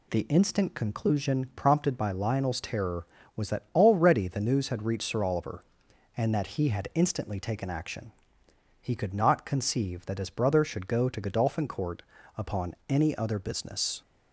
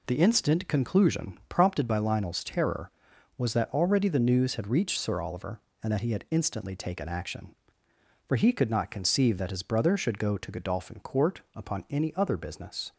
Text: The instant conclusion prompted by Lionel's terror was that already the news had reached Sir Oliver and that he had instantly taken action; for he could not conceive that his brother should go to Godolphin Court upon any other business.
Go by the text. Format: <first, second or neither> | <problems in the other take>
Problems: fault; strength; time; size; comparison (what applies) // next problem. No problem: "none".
second | skips "for"; at 8.4 s // pauses between "Court" and "upon"; slight; at 12.0 s; 0.34 s long